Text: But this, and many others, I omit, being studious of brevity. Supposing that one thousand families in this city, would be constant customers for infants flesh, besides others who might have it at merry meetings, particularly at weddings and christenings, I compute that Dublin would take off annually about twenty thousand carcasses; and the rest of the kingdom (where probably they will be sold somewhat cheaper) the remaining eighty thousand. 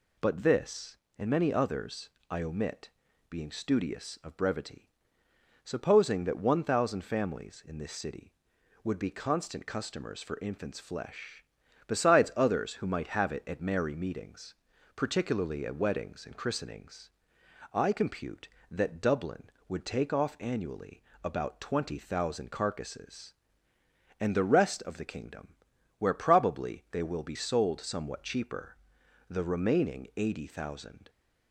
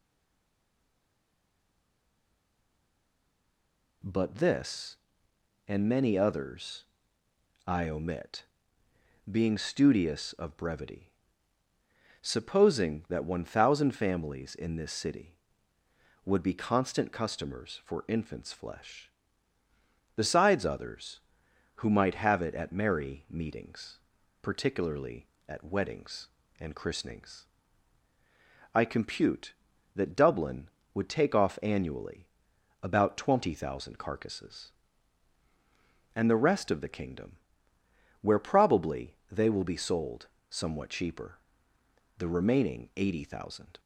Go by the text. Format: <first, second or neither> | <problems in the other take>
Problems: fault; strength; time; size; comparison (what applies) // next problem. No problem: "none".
first | stays silent before the first word; strong; until 4.0 s; 4.0 s long // pauses between "annually" and "about"; noticeable; at 32.2 s; 0.58 s long; slight in the first // pauses between "probably" and "they"; slight; at 39.1 s; 0.18 s long // pauses between "sold" and "somewhat"; slight; at 40.2 s; 0.22 s long